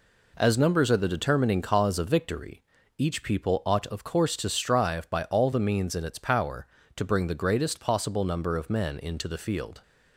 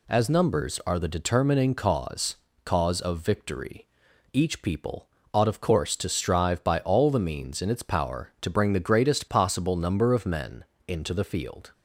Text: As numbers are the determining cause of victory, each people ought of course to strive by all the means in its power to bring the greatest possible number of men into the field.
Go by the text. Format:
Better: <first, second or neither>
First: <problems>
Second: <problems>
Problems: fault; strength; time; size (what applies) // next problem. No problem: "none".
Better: first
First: none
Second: says "cause" twice; at 2.6 s // pauses between "people" and "ought"; slight; at 5.0 s; 0.26 s long // pauses between "men" and "into"; slight; at 10.6 s; 0.22 s long